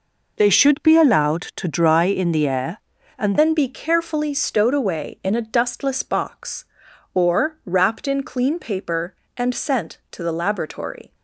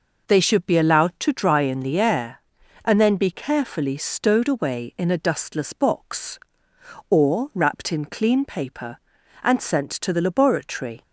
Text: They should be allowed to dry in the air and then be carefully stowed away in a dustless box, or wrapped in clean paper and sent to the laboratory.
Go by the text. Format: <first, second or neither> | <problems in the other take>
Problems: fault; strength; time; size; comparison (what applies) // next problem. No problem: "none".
second | changes voice at "then"; from 3.3 s on; 7.8 s long